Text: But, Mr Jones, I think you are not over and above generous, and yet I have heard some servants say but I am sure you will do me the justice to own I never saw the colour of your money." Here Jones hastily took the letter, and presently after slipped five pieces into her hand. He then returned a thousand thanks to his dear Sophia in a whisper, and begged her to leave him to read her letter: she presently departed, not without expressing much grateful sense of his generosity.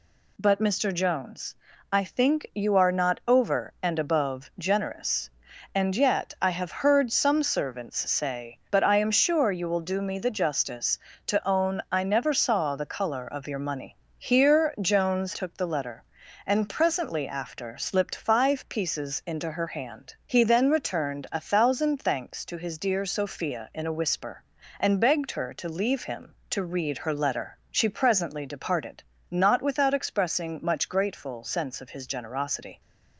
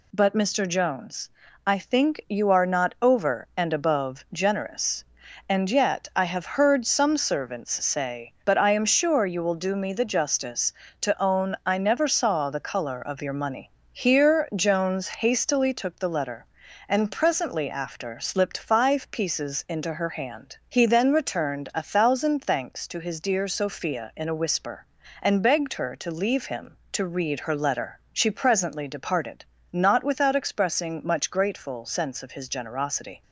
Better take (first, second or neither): second